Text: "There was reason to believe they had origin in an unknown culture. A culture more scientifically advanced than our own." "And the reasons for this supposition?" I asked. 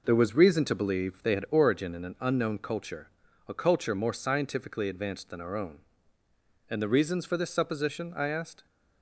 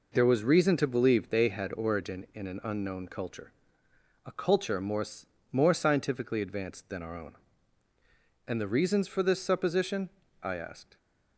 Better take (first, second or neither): first